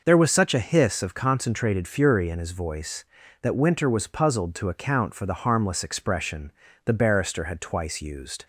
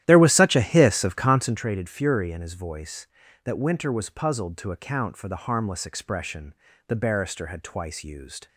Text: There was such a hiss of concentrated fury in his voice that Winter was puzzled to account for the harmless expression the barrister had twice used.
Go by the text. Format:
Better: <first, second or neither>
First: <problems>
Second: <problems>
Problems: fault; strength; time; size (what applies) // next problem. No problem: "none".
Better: first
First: pauses between "expression" and "the"; slight; at 6.5 s; 0.34 s long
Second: starts louder than the rest; strong; until 1.6 s; 12.5 dB // pauses between "expression" and "the"; slight; at 6.5 s; 0.34 s long